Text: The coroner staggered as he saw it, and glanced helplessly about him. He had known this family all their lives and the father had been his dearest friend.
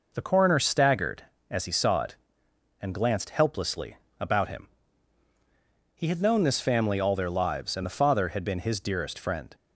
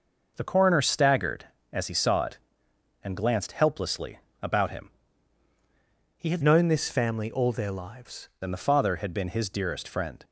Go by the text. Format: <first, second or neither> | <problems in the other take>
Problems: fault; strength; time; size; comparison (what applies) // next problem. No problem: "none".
first | pauses between "helplessly" and "about"; slight; at 4.1 s; 0.24 s long; slight in the first // changes voice from "known" to "lives"; from 6.4 to 8.2 s; 1.8 s long